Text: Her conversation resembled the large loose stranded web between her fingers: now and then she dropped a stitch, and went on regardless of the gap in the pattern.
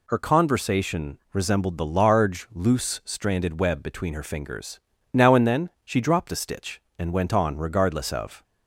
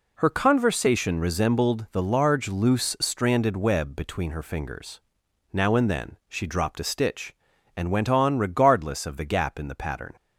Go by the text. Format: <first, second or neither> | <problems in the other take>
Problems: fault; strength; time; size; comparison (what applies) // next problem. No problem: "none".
second | pauses between "conversation" and "resembled"; slight; at 1.1 s; 0.16 s long // stops before "the gap in the pattern"; at 8.4 s